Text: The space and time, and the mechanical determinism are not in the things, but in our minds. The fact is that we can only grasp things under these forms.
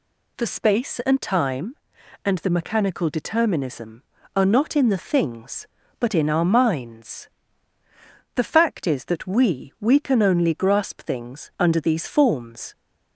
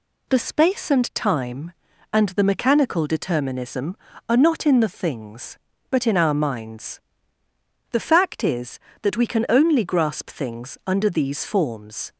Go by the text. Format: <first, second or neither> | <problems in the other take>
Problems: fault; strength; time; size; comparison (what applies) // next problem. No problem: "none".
second | says "we" twice; at 9.7 s